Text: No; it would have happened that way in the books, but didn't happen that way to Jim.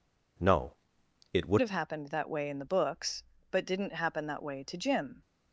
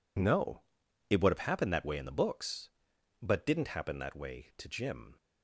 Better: second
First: changes voice at "have"; from 1.6 s on; 3.6 s long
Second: none

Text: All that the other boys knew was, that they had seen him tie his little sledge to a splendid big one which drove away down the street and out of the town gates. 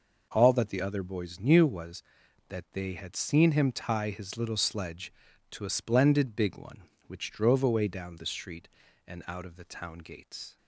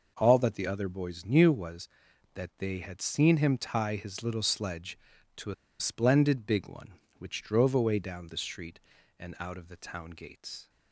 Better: first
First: none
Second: pauses between "a" and "splendid"; slight; at 5.5 s; 0.26 s long

